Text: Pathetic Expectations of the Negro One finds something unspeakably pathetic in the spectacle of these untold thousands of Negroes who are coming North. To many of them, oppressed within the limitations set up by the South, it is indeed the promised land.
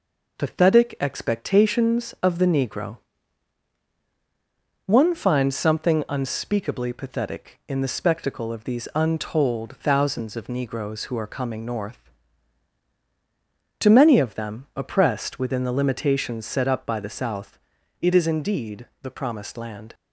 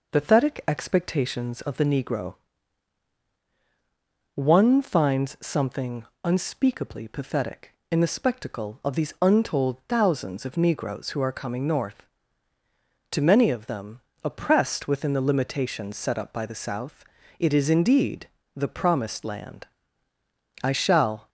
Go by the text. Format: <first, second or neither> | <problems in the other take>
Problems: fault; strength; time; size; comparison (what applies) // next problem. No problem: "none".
first | pauses between "Negro" and "One"; strong; at 2.3 s; 2.0 s long; strong in the first // pauses between "something" and "unspeakably"; slight; at 6.0 s; 0.20 s long // pauses between "indeed" and "the"; slight; at 18.2 s; 0.28 s long; slight in the first // goes on to say "I shall"; noticeable; from 20.6 s on; 0.66 s long